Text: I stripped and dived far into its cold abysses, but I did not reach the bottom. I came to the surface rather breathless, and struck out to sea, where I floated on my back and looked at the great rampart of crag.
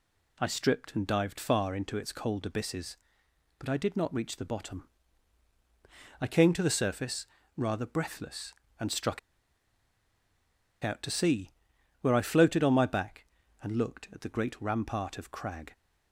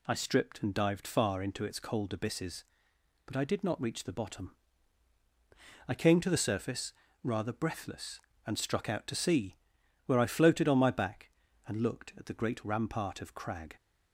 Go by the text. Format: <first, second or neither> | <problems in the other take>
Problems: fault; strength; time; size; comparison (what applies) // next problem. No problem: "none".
second | pauses between "surface" and "rather"; slight; at 7.2 s; 0.30 s long; slight in the second // pauses between "struck" and "out"; strong; at 9.1 s; 1.6 s long